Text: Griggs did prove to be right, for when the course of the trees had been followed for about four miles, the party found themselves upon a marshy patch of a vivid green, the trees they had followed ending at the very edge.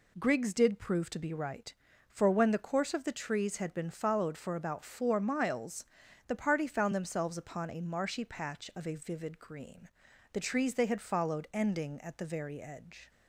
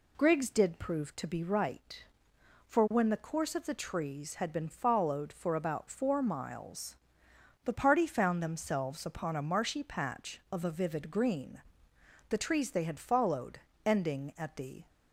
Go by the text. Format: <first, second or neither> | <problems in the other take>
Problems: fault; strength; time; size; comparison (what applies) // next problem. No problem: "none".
first | pauses between "followed" and "ending"; slight; at 13.5 s; 0.26 s long // stops before "very edge"; at 14.8 s